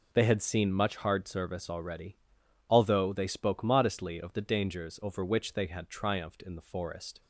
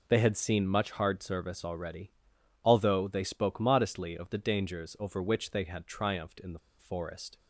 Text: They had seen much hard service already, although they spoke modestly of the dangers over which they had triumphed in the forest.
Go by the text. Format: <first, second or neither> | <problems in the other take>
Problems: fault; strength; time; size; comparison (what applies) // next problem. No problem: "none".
first | pauses between "the" and "forest"; slight; at 6.5 s; 0.20 s long